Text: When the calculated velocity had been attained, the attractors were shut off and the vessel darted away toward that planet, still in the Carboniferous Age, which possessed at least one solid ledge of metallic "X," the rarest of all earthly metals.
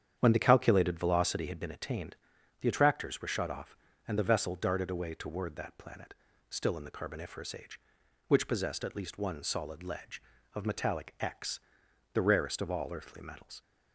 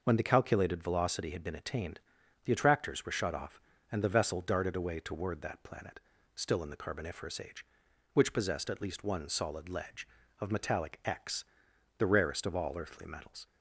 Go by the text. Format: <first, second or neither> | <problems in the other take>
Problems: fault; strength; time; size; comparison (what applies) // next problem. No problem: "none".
second | starts louder than the rest; strong; until 1.8 s; 9 dB